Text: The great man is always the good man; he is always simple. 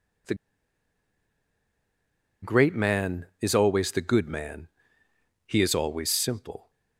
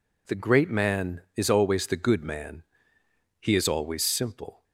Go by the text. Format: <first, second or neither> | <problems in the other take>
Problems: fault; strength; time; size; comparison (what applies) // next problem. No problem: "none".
second | pauses between "The" and "great"; strong; at 0.3 s; 2.0 s long